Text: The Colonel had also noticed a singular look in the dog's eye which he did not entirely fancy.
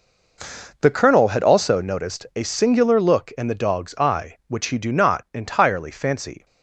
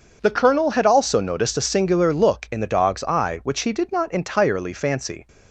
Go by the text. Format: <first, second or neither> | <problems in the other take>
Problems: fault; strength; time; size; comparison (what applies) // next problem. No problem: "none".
second | says "do" for "did"; at 4.7 s